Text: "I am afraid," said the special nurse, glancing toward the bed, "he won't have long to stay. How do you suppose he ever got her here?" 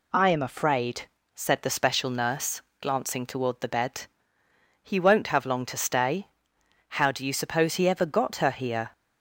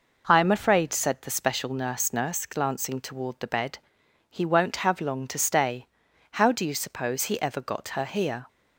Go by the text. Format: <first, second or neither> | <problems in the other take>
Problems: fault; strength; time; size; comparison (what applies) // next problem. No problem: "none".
first | says "nurse" twice; at 2.1 s